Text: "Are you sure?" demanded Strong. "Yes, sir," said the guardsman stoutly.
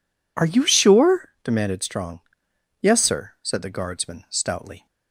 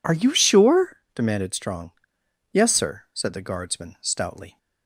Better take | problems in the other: neither | none

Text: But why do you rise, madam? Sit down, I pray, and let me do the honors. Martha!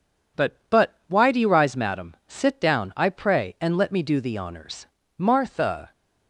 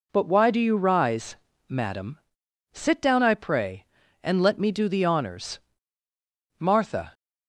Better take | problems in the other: second | says "But" twice; at 0.6 s

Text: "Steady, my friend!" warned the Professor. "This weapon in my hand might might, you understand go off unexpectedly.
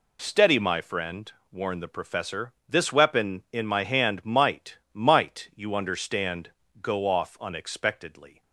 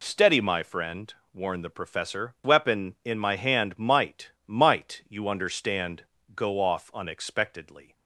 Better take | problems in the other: first | skips "This"; at 2.3 s // pauses between "might" and "might"; slight; at 4.3 s; 0.16 s long; slight in the first // pauses between "understand" and "go"; slight; at 6.0 s; 0.30 s long; slight in the first

